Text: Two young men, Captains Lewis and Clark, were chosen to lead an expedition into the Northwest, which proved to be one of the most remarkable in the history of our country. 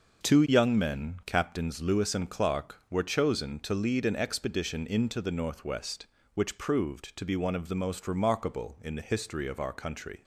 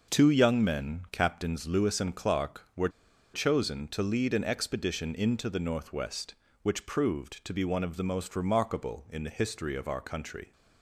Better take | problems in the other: first | pauses between "were" and "chosen"; at 2.8 s; 0.44 s long

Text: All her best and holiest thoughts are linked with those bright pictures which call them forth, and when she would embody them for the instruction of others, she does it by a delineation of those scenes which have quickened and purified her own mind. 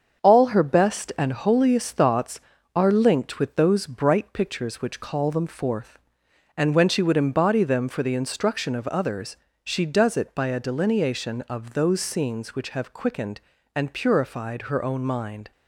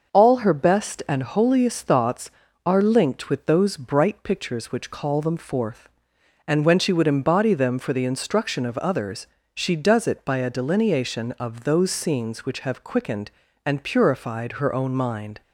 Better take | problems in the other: second | gets quieter; noticeable; throughout; 5 dB // starts louder than the rest; until 1.2 s; 7 dB; noticeable in the second

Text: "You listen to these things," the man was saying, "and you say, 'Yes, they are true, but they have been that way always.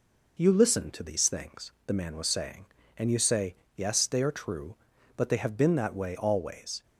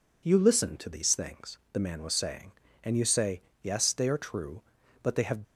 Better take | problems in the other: first | stops before "been that way always"; at 5.4 s

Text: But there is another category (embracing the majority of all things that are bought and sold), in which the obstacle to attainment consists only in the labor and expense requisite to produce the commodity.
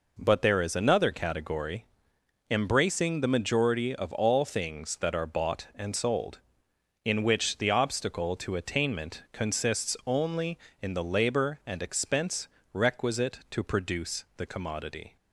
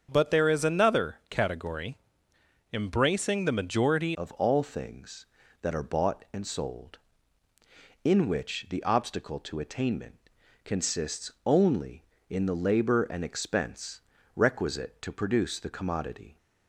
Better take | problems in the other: first | starts louder than the rest; strong; until 1.1 s; 7 dB // changes voice at "of"; from 4.1 s on; 12.2 s long // pauses between "attainment" and "consists"; at 10.1 s; 0.44 s long // pauses between "expense" and "requisite"; slight; at 14.0 s; 0.36 s long; slight in the first

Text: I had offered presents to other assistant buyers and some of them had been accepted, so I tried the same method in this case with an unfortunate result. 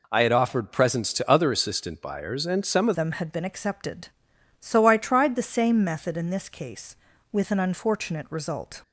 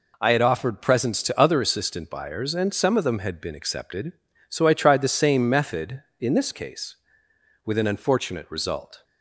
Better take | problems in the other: second | changes voice at "them"; from 2.9 s on; 5.9 s long

